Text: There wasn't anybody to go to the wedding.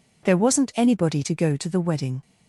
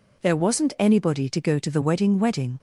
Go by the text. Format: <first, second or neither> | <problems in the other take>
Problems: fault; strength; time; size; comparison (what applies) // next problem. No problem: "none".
first | says "wedding" twice; at 2.1 s